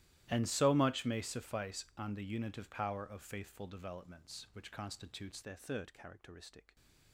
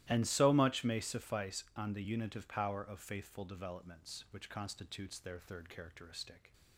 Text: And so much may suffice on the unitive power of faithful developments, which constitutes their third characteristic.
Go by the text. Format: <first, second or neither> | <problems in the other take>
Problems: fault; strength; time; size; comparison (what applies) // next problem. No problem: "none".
second | starts louder than the rest; strong; until 1.3 s; 14.5 dB; strong in the second // changes voice at "their"; from 5.4 s on; 1.3 s long